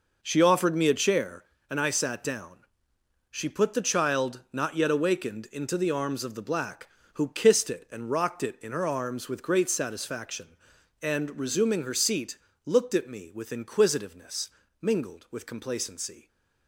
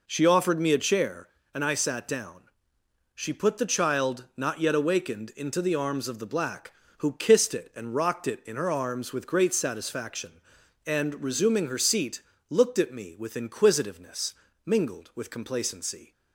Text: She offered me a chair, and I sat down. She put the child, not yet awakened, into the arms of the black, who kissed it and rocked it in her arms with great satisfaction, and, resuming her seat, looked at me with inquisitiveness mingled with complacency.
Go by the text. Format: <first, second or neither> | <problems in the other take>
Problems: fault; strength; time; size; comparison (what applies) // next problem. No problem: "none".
second | gets quieter; strong; throughout; 10.5 dB // pauses between "inquisitiveness" and "mingled"; slight; at 14.4 s; 0.34 s long; slight in the second